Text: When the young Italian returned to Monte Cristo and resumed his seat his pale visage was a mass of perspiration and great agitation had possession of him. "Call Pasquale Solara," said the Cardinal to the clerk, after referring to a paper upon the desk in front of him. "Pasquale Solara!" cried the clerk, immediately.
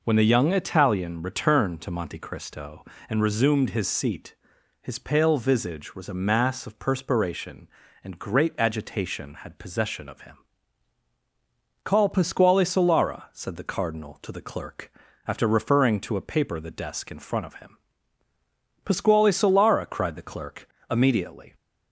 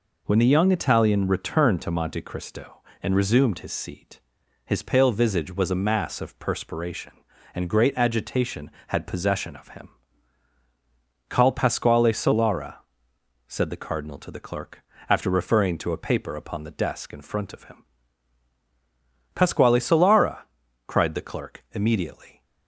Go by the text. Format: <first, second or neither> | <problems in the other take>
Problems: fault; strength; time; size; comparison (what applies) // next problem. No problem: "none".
second | pauses between "seat" and "his"; noticeable; at 4.3 s; 0.48 s long; also in the second // skips "upon"; at 16.6 s